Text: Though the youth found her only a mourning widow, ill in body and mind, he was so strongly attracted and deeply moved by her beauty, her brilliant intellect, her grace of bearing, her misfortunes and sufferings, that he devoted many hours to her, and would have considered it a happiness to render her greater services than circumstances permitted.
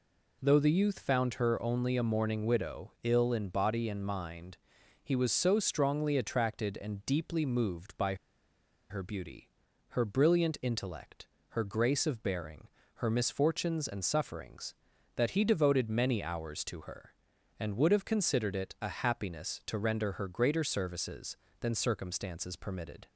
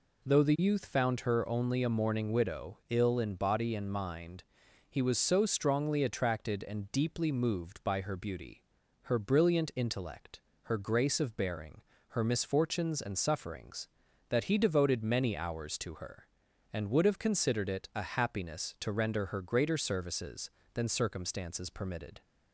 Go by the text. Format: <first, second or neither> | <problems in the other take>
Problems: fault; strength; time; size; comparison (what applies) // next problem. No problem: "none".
second | pauses between "by" and "her"; noticeable; at 8.1 s; 0.75 s long